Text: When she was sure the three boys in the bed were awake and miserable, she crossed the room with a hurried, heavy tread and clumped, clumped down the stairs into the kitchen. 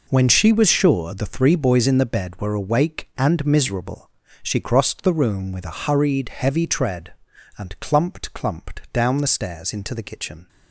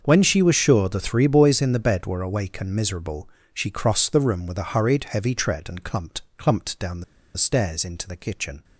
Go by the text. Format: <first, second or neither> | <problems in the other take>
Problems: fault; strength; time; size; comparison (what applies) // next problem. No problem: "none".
first | starts louder than the rest; until 1.0 s; 6.5 dB // pauses between "the" and "stairs"; slight; at 7.0 s; 0.33 s long